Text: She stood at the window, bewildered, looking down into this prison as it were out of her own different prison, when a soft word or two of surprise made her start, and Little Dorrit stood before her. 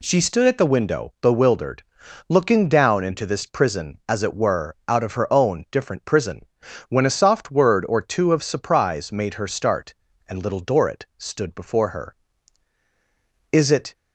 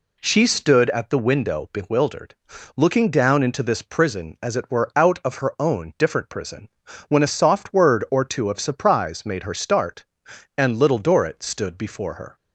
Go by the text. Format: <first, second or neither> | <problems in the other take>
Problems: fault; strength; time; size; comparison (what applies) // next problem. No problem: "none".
second | goes on to say "Is it"; slight; from 13.5 s on; 0.42 s long